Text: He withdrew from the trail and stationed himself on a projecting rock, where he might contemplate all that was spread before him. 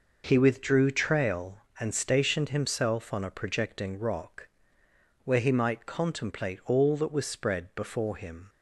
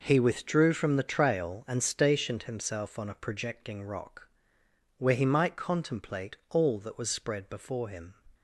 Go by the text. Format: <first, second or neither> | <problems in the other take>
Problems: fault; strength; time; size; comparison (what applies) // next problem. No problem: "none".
second | skips "from the"; at 0.8 s